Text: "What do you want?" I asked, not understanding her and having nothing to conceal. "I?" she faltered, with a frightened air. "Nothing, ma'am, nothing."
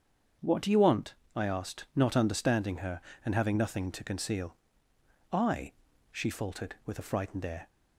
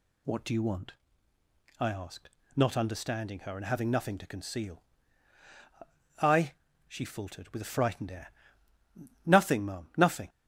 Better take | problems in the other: second | starts louder than the rest; strong; until 1.6 s; 7 dB // stops before "Nothing ma'am nothing"; at 7.6 s

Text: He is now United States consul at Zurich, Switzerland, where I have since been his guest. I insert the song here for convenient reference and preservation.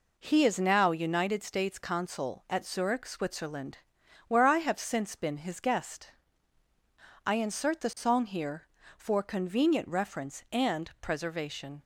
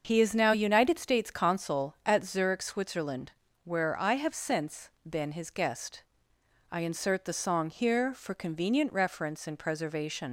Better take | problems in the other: first | starts louder than the rest; until 1.0 s; 6.5 dB // pauses between "since" and "been"; slight; at 4.8 s; 0.18 s long // leaves "preservation" unfinished; at 10.2 s; 110 ms

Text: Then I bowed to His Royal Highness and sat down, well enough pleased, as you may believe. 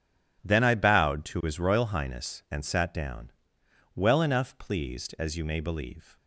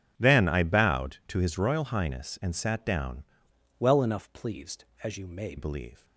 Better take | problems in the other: first | changes voice from "well" to "may"; from 3.7 to 5.5 s; 1.8 s long

